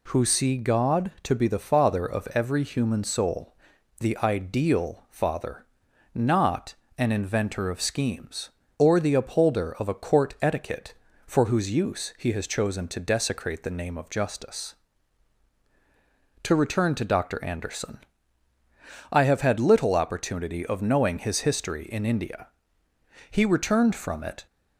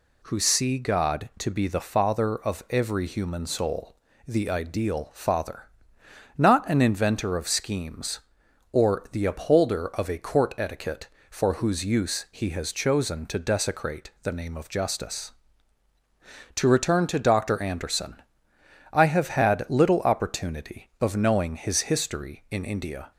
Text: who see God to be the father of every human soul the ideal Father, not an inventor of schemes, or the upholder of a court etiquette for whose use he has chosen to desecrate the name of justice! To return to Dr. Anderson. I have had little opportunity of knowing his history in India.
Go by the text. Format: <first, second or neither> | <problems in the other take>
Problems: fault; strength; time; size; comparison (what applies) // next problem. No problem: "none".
second | pauses between "soul" and "the"; at 3.5 s; 0.44 s long; slight in the second // pauses between "not" and "an"; slight; at 6.7 s; 0.24 s long // goes on to say "He returned from it"; noticeable; from 23.3 s on; 1.1 s long